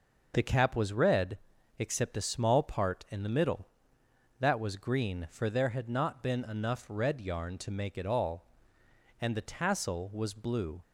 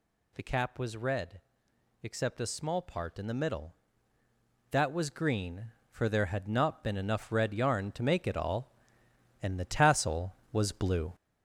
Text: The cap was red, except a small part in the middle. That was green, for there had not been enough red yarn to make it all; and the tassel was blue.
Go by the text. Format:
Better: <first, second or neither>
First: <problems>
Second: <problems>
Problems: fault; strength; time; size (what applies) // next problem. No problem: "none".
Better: first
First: none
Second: gets louder; noticeable; throughout; 5.5 dB